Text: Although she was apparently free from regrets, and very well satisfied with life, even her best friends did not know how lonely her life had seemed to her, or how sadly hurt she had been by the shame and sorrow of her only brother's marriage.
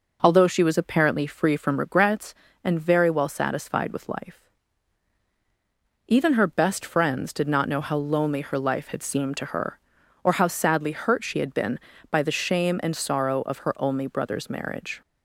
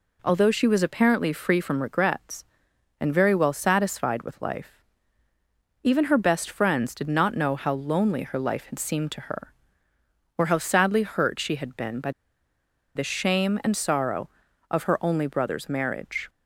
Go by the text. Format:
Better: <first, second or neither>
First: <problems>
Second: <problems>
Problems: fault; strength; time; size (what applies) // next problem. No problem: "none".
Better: first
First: none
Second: pauses between "by" and "the"; noticeable; at 12.1 s; 0.84 s long